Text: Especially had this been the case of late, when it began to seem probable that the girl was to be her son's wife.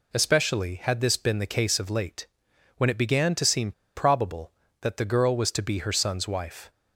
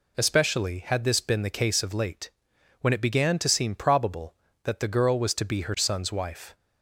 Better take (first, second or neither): second